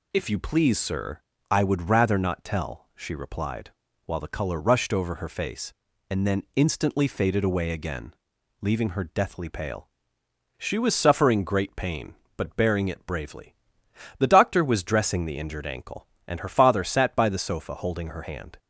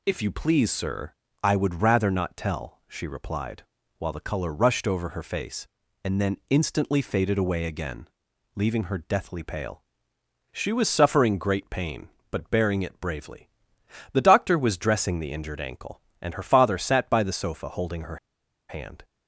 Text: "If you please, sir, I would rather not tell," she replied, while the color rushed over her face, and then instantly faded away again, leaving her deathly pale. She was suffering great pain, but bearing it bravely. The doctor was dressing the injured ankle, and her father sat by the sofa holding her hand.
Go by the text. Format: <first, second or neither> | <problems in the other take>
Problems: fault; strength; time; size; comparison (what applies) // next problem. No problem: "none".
first | pauses between "her" and "hand"; noticeable; at 18.1 s; 0.53 s long